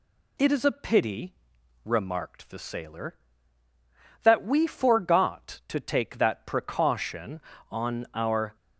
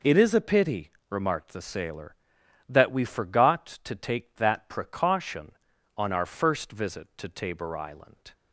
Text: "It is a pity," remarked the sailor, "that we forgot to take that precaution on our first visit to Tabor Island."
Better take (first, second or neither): second